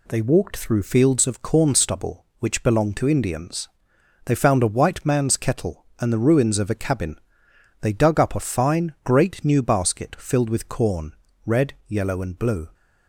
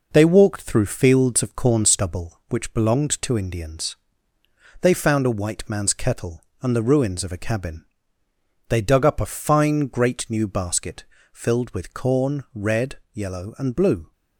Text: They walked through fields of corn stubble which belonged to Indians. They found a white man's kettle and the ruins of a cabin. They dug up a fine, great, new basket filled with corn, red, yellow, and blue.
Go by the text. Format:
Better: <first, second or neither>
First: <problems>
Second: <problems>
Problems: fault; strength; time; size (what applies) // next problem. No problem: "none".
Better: first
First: none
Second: gets quieter; noticeable; throughout; 5 dB // pauses between "basket" and "filled"; slight; at 11.0 s; 0.28 s long